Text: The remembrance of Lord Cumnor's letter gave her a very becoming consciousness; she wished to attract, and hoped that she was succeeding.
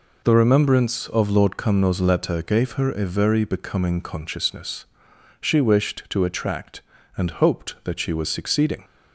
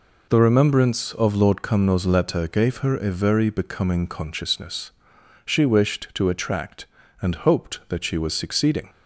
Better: neither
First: none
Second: none

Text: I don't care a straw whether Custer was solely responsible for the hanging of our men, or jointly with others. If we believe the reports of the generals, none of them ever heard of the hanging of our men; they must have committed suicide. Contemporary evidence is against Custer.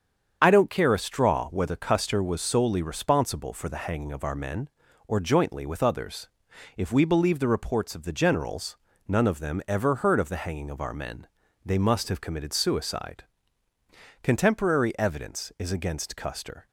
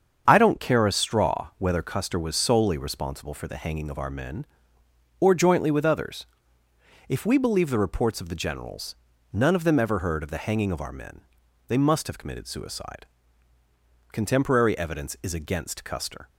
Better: neither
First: starts louder than the rest; strong; until 1.4 s; 7.5 dB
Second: starts louder than the rest; until 1.2 s; 7 dB

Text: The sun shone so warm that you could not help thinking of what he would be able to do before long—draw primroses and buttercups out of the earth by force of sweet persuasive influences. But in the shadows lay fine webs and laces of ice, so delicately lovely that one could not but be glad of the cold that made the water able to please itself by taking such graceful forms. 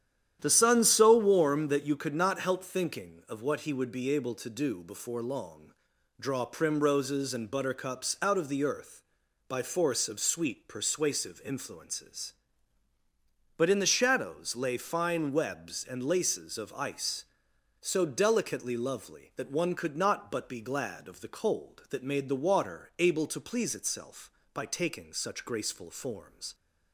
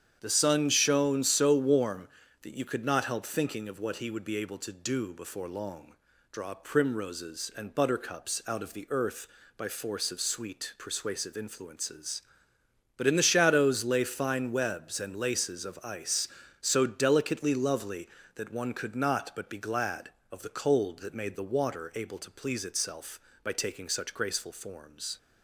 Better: second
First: starts louder than the rest; strong; until 1.4 s; 10.5 dB // skips "shone"; at 0.8 s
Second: starts louder than the rest; strong; until 1.2 s; 8.5 dB

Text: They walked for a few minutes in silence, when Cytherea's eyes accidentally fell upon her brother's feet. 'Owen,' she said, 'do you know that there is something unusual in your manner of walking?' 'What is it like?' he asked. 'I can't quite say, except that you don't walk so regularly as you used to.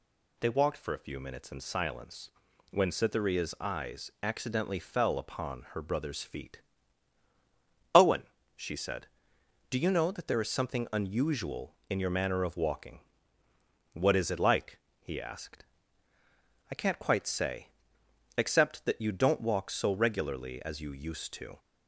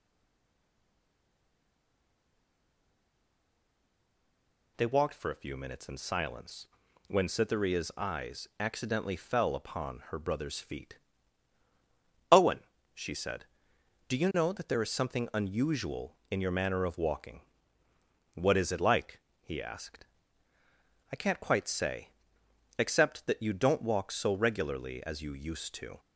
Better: first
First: none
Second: stays silent before the first word; strong; until 4.7 s; 4.7 s long

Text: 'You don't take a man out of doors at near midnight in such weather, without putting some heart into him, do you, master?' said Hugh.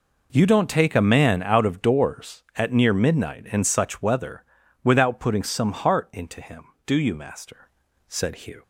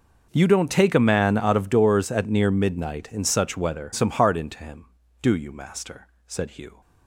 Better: first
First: none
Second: skips "without putting"; at 3.9 s

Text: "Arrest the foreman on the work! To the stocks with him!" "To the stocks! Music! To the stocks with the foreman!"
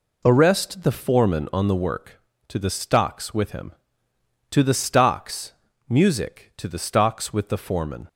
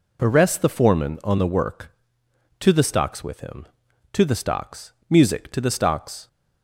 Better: first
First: none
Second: stops before "with the foreman"; at 6.2 s

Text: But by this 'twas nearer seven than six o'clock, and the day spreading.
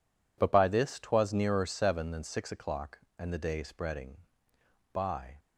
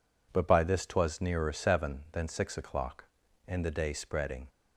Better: second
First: goes on to say "By"; slight; from 4.9 s on; 0.46 s long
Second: none

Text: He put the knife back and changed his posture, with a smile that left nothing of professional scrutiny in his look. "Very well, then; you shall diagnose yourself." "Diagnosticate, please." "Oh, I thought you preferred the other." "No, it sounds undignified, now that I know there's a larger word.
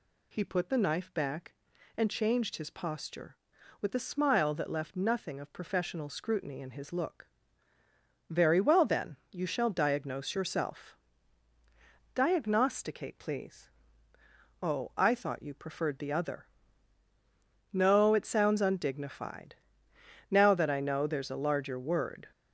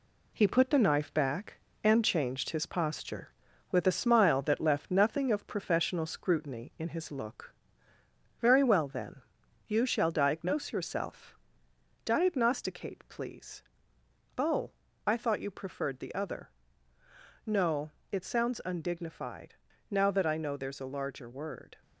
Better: first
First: none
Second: gets quieter; noticeable; throughout; 4.5 dB

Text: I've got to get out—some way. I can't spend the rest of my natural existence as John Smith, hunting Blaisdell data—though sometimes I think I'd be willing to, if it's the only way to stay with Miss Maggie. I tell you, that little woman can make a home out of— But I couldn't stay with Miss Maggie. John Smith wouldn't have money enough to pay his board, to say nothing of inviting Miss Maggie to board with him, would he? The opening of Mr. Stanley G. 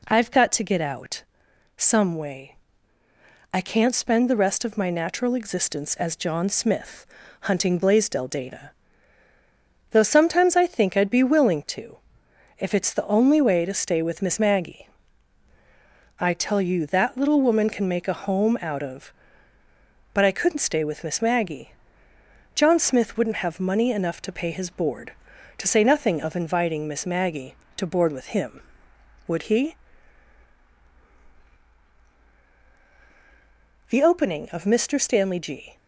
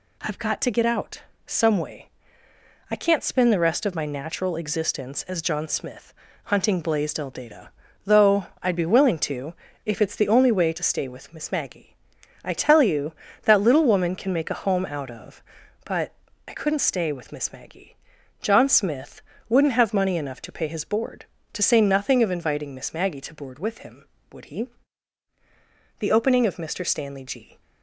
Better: first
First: none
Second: skips "sometimes I think"; at 8.5 s // pauses between "But" and "I"; slight; at 16.1 s; 0.34 s long // pauses between "Smith" and "wouldn't"; slight; at 19.2 s; 0.28 s long

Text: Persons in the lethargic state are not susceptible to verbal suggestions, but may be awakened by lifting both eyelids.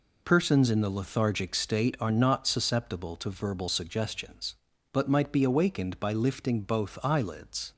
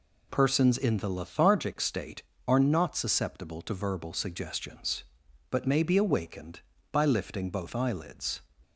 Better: second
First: says "might" for "may"; at 5.0 s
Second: none

